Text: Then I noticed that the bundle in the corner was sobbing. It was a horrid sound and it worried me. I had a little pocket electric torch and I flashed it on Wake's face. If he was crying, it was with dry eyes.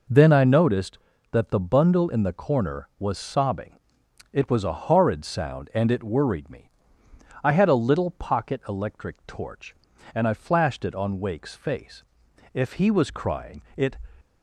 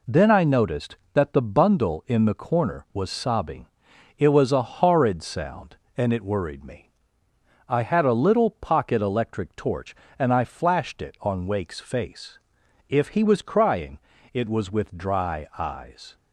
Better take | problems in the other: second | stops before "was with dry eyes"; at 14.2 s

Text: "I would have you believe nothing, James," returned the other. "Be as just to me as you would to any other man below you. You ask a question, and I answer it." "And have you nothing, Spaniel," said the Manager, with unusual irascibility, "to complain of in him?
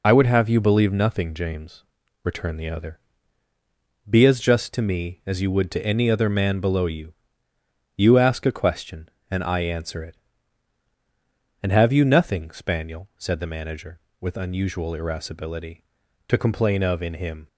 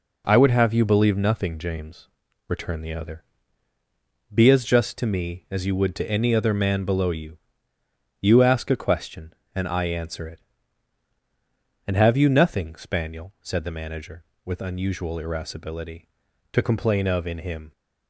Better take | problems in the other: second | loses the start of "I"; at 0.0 s; 45 ms

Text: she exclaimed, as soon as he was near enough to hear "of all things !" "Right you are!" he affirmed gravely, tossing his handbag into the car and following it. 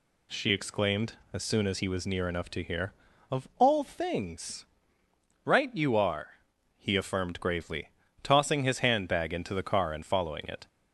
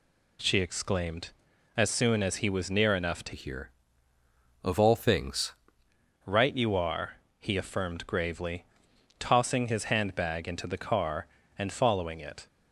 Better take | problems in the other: first | changes voice from "hear" to "things"; from 3.3 to 5.5 s; 2.2 s long

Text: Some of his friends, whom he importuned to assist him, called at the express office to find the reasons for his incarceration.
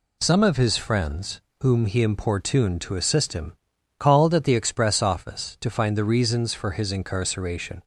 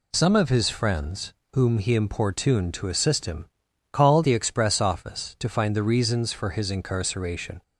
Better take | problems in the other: first | skips "at"; at 4.2 s

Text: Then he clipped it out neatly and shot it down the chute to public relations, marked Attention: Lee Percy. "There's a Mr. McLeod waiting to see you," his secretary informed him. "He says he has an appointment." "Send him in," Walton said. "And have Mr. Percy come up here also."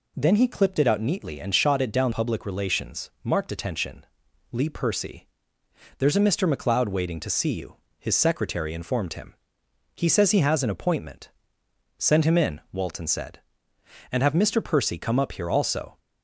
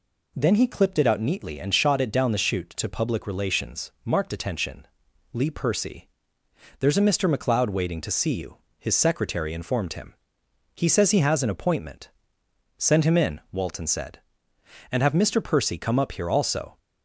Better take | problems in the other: second | skips "the chute to"; at 2.1 s

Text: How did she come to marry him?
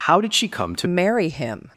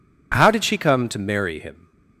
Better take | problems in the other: second | changes voice at "marry"; from 0.8 s on; 0.9 s long

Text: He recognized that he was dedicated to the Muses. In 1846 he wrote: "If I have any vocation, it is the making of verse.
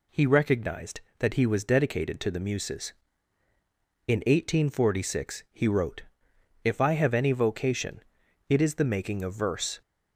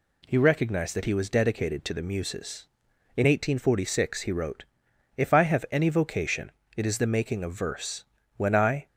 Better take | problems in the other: first | goes on to say "When I"; from 8.3 s on; 0.50 s long

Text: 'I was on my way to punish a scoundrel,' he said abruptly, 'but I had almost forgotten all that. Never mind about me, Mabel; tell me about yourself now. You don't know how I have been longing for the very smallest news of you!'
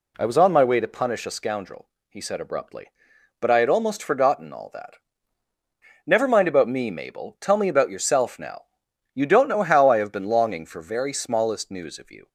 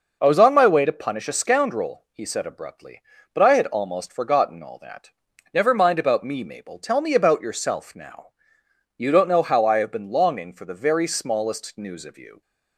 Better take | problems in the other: second | skips "the"; at 10.7 s

